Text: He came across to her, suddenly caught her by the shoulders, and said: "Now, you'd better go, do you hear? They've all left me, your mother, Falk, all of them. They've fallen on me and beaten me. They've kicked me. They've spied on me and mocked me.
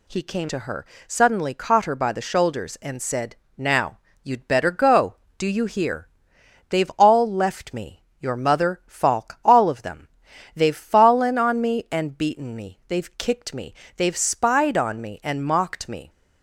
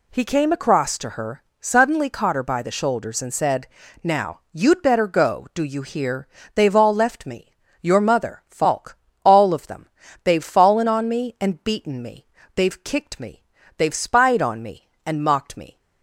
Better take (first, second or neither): second